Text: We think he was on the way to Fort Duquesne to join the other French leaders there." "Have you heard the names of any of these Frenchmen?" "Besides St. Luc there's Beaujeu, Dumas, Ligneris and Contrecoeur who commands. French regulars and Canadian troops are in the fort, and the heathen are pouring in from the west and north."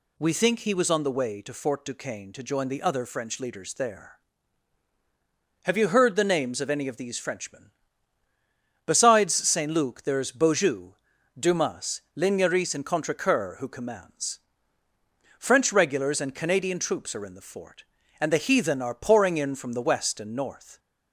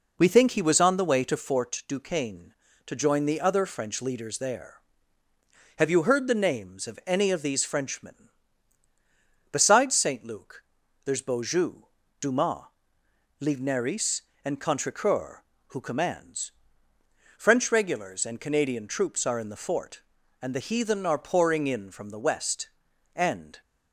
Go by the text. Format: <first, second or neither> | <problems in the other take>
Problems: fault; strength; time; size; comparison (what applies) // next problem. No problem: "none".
first | pauses between "Luc" and "there's"; at 10.6 s; 0.42 s long // stops before "north"; at 23.6 s